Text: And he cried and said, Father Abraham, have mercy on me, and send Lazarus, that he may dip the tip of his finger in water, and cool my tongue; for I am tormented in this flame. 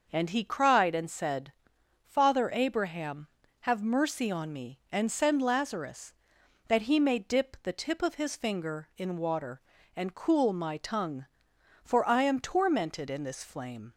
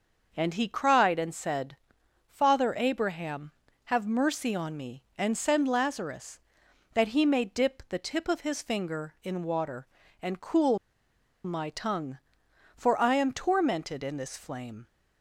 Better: first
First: starts louder than the rest; noticeable; until 1.1 s; 6 dB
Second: starts louder than the rest; noticeable; until 1.3 s; 6 dB // pauses between "cool" and "my"; noticeable; at 10.7 s; 0.67 s long

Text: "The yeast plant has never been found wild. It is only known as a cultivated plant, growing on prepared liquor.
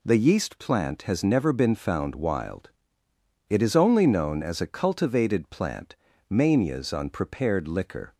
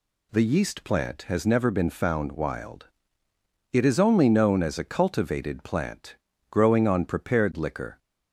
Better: second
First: says "manias" for "growing"; at 6.2 s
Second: none

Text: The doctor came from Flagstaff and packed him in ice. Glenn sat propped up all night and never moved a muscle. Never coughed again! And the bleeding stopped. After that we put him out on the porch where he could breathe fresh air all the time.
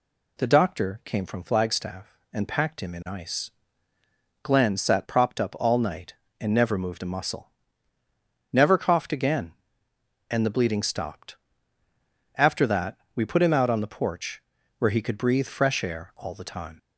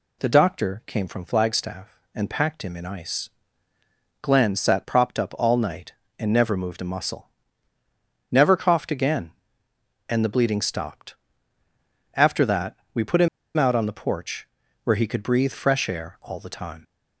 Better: first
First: pauses between "that" and "we"; slight; at 12.9 s; 0.18 s long // pauses between "porch" and "where"; slight; at 14.4 s; 0.36 s long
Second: pauses between "that" and "we"; slight; at 12.7 s; 0.18 s long // pauses between "him" and "out"; slight; at 13.2 s; 0.28 s long // pauses between "porch" and "where"; slight; at 14.4 s; 0.36 s long

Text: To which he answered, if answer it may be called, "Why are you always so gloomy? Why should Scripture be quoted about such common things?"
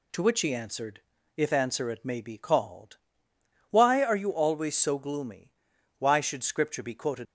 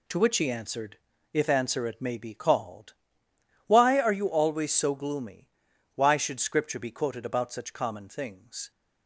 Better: second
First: stops before "about such common things"; at 7.2 s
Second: none

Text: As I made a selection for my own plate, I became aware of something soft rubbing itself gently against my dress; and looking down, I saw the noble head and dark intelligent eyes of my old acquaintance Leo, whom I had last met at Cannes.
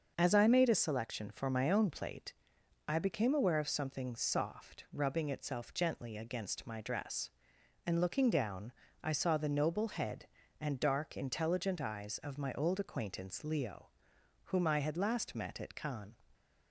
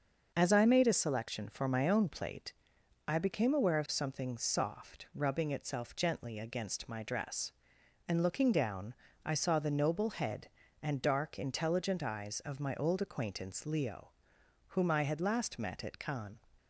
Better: neither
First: starts louder than the rest; until 1.1 s; 6.5 dB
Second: starts louder than the rest; until 1.3 s; 6.5 dB

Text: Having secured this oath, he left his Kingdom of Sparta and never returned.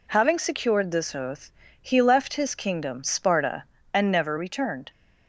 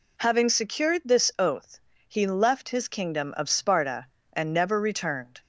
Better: second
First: skips "of"; at 3.0 s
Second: none

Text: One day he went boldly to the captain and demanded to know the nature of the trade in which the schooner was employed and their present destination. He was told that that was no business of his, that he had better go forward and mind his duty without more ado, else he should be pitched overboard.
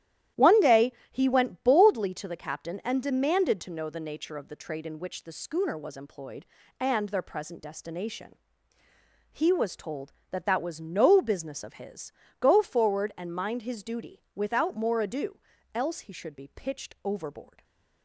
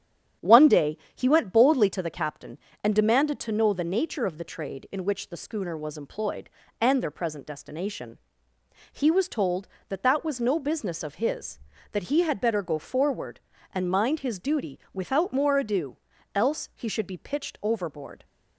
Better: second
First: starts louder than the rest; strong; until 1.5 s; 12 dB // pauses between "day" and "he"; slight; at 0.9 s; 0.20 s long // skips "that he had better"; at 12.2 s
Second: starts louder than the rest; strong; until 1.5 s; 9 dB // pauses between "day" and "he"; slight; at 0.9 s; 0.18 s long

